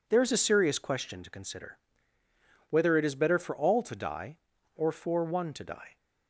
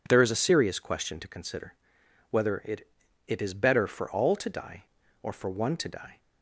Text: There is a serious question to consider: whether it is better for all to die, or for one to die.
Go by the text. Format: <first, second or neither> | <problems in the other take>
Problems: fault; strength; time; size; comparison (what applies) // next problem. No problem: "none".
first | says "it" twice; at 3.2 s